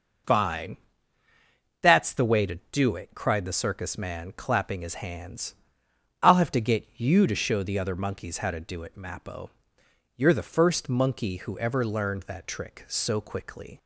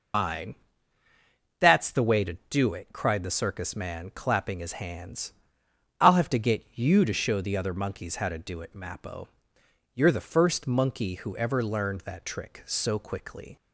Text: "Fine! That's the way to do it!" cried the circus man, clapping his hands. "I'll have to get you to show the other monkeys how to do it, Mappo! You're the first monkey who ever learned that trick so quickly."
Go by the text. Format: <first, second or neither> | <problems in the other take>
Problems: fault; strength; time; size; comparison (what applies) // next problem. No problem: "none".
first | loses the start of "Fine"; at 0.1 s; 110 ms